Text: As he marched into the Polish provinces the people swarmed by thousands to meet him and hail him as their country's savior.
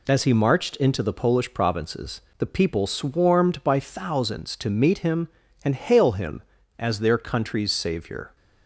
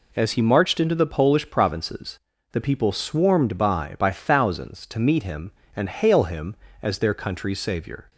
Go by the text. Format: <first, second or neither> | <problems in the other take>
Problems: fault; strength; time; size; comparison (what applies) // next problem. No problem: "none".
first | pauses between "provinces" and "the"; slight; at 2.1 s; 0.34 s long; slight in the first // says "by" twice; at 3.9 s